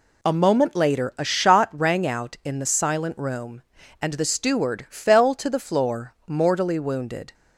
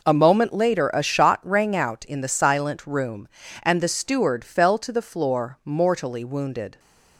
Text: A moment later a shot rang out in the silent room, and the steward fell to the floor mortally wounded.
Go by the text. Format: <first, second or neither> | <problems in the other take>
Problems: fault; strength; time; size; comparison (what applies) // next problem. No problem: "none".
neither | none